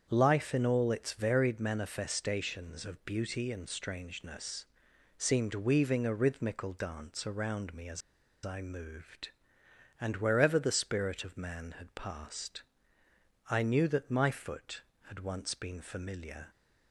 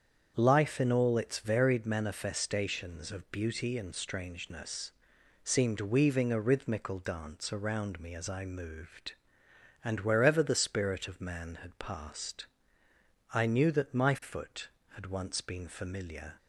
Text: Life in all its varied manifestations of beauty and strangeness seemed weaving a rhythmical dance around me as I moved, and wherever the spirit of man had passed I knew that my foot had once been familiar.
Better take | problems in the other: second | starts louder than the rest; strong; until 1.1 s; 7.5 dB; strong in the second // pauses between "strangeness" and "seemed"; noticeable; at 4.6 s; 0.54 s long; noticeable in the second // pauses between "as" and "I"; at 8.0 s; 0.43 s long // pauses between "passed" and "I"; noticeable; at 12.6 s; 0.86 s long; noticeable in the second

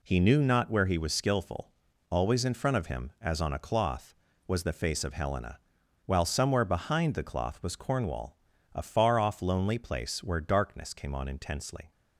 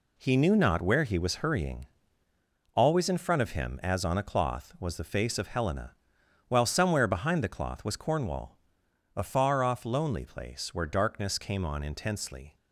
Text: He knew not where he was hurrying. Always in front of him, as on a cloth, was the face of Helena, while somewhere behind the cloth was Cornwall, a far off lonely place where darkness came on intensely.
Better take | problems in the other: second | says "skillful" for "hurrying"; at 1.1 s

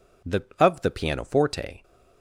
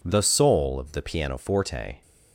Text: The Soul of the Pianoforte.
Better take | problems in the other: second | skips "Soul"; at 0.5 s

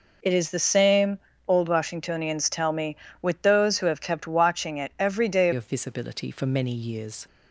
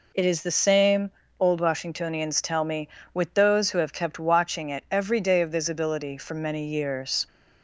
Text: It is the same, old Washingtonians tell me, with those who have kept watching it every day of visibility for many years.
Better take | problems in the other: second | changes voice at "of"; from 5.5 s on; 1.7 s long

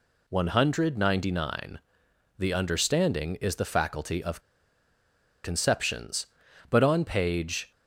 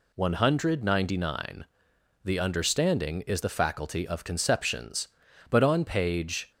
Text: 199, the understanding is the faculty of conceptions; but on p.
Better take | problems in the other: second | pauses between "of" and "conceptions"; at 4.4 s; 1.0 s long

